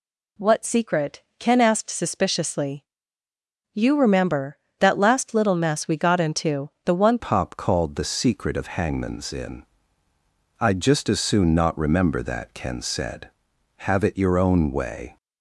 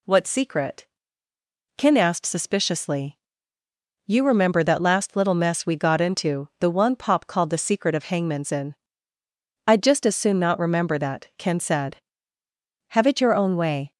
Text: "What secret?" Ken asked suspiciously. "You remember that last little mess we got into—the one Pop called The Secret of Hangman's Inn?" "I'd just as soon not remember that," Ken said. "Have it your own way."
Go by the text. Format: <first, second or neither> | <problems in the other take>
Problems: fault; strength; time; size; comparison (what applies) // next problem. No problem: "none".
second | changes voice at "Pop"; from 7.1 s on; 8.0 s long